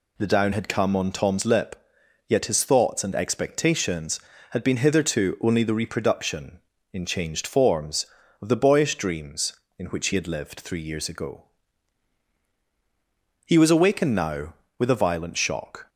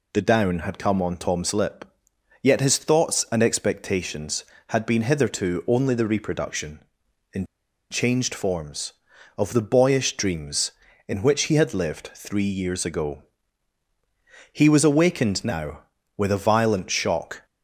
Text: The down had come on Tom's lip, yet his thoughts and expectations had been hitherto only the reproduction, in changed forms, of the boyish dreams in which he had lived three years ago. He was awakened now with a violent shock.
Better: first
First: none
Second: pauses between "in" and "changed"; at 7.4 s; 0.45 s long

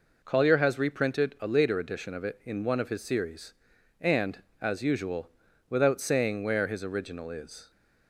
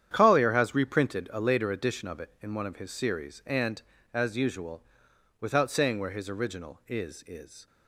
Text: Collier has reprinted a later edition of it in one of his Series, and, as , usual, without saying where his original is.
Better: first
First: none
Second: starts louder than the rest; strong; until 1.1 s; 9.5 dB // says "is" twice; at 7.2 s

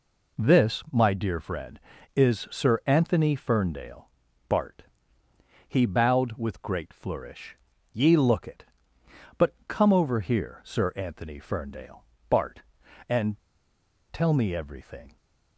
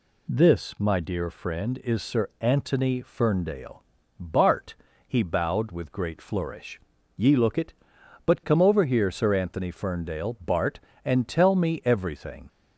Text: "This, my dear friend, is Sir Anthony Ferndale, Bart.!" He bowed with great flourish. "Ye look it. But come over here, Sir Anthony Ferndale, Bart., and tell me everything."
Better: second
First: pauses between "and" and "tell"; noticeable; at 13.3 s; 0.76 s long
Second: none

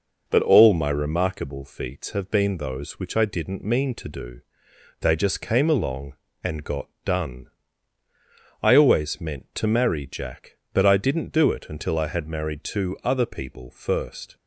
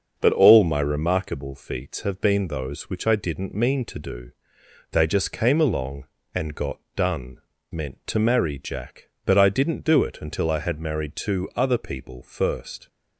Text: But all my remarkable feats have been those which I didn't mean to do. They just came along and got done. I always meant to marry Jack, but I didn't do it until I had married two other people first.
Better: first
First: pauses between "got" and "done"; slight; at 6.8 s; 0.16 s long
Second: starts louder than the rest; until 1.1 s; 6.5 dB // pauses between "got" and "done"; slight; at 6.7 s; 0.16 s long // skips "I always"; at 7.5 s

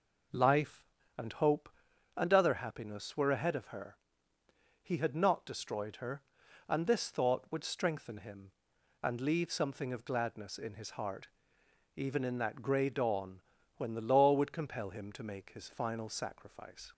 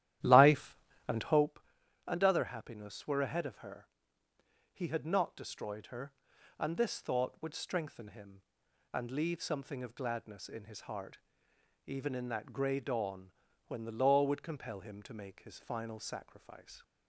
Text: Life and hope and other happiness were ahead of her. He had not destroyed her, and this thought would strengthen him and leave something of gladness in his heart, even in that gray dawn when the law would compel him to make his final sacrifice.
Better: first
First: pauses between "dawn" and "when"; at 13.4 s; 0.38 s long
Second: starts louder than the rest; strong; until 1.5 s; 12.5 dB // pauses between "dawn" and "when"; at 13.3 s; 0.38 s long

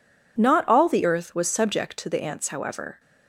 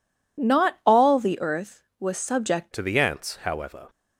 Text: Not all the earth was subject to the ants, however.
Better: first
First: none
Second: changes voice at "to"; from 2.7 s on; 1.1 s long

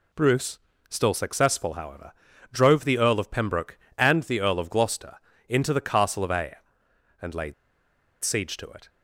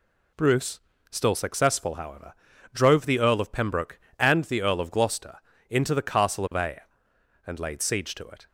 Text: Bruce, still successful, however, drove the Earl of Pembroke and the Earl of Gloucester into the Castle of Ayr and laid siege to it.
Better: second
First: pauses between "Gloucester" and "into"; slight; at 5.1 s; 0.32 s long // pauses between "laid" and "siege"; noticeable; at 7.5 s; 0.68 s long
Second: pauses between "Gloucester" and "into"; slight; at 5.3 s; 0.32 s long

